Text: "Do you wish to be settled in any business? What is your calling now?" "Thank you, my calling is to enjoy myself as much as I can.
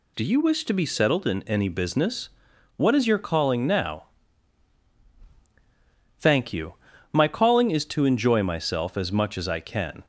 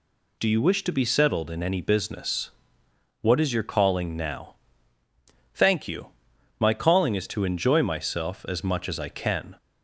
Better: neither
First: none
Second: none

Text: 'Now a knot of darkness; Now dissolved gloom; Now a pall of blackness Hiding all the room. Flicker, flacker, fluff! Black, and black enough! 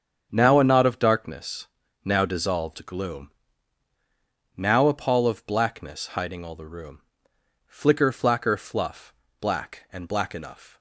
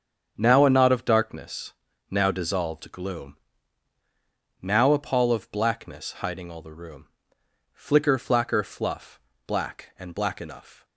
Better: neither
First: starts louder than the rest; strong; until 1.3 s; 7.5 dB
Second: starts louder than the rest; strong; until 1.3 s; 7.5 dB

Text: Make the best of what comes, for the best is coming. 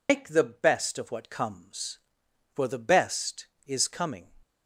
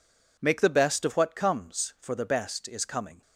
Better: second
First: loses the start of "Make"; at 0.0 s; 115 ms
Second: none

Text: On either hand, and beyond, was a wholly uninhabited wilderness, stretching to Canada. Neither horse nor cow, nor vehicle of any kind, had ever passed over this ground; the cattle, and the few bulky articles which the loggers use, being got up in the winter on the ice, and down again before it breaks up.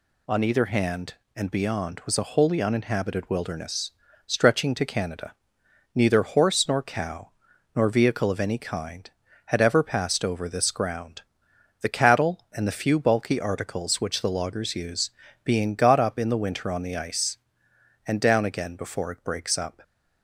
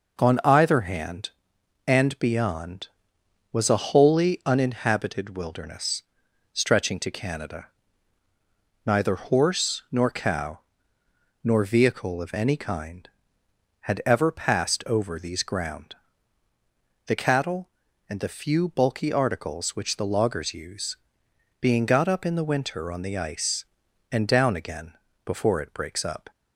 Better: first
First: none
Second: says "these" for "this"; at 15.1 s // pauses between "again" and "before"; slight; at 24.9 s; 0.30 s long

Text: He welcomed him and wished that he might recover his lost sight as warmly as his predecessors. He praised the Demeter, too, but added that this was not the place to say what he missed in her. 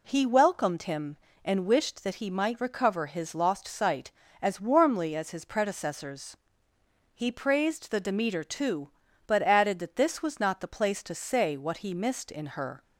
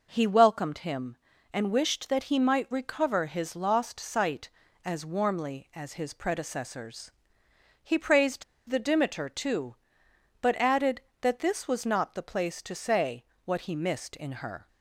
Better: first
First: none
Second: pauses between "praised" and "the"; slight; at 8.4 s; 0.25 s long // pauses between "say" and "what"; slight; at 13.2 s; 0.18 s long

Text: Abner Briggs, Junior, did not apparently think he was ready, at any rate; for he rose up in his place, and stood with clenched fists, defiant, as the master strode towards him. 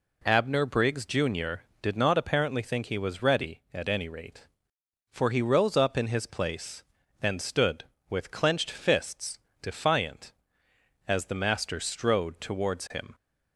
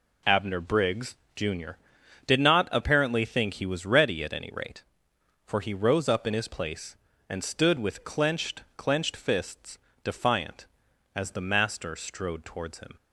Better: first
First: none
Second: says "clenched" twice; at 8.7 s

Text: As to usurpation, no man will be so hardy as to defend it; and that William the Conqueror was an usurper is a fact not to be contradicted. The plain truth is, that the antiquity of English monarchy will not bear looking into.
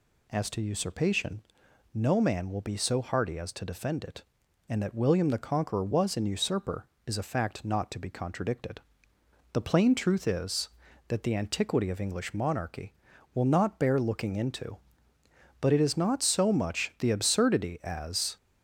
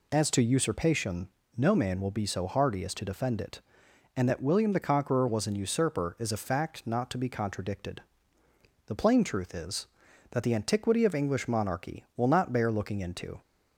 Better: second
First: goes on to say "But it is not so much the absurdity as"; strong; from 15.6 s on; 2.7 s long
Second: none

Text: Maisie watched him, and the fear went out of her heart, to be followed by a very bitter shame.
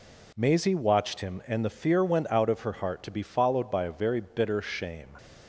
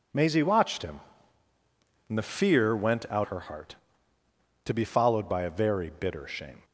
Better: first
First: none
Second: skips "of"; at 3.2 s

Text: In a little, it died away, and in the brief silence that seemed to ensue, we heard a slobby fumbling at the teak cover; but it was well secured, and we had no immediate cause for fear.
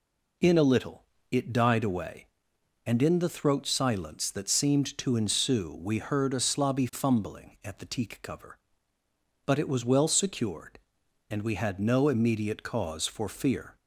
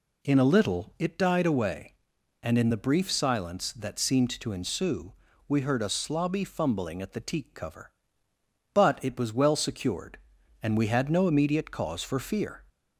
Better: second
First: says "throat" for "brief"; at 3.2 s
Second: none

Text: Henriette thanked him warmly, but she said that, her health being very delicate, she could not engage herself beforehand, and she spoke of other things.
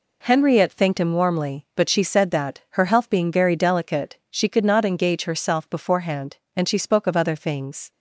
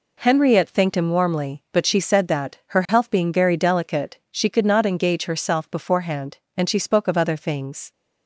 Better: neither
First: none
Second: none

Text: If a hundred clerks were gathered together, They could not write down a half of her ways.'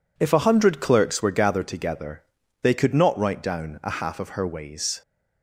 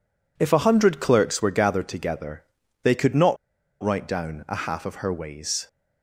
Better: first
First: none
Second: pauses between "not" and "write"; noticeable; at 3.3 s; 0.47 s long

